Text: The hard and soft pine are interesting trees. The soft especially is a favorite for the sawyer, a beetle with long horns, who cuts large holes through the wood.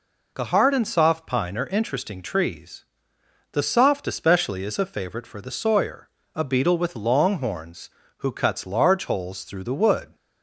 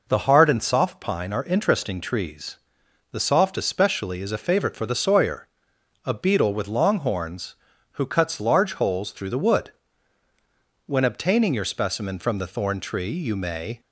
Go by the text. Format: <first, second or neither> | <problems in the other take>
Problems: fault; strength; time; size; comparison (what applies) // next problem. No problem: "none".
first | goes on to say "When obtaining your specimen from the thorn tree you may"; strong; from 10.8 s on; 2.9 s long